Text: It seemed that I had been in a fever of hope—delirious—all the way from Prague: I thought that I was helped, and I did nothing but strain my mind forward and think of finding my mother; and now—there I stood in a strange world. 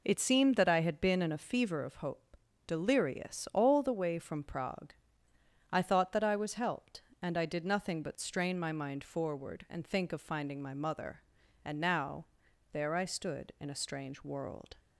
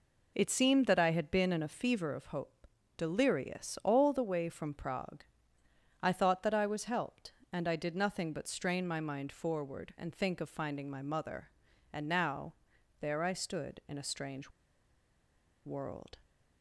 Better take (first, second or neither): first